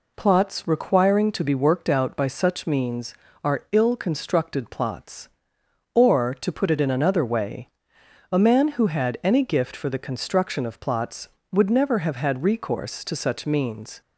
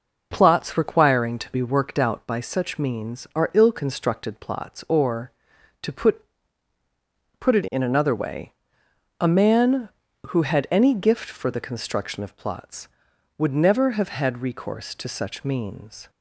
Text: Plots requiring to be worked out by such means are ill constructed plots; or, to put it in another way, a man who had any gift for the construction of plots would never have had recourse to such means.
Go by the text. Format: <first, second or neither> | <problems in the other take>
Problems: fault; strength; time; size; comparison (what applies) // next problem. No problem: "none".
first | says "put" twice; at 7.3 s